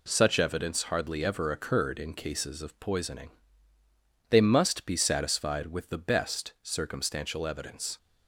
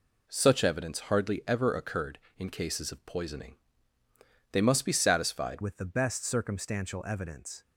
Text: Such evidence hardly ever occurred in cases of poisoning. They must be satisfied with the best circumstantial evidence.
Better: first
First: none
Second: changes voice at "with"; from 5.6 s on; 2.0 s long

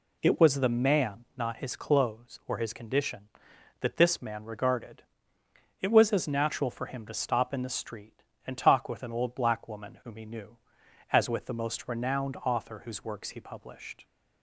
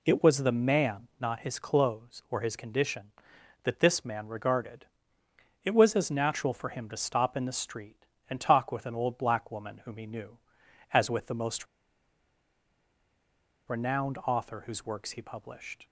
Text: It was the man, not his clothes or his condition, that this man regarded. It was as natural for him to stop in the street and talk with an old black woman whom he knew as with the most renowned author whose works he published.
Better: first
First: none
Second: pauses between "most" and "renowned"; strong; at 11.6 s; 2.0 s long

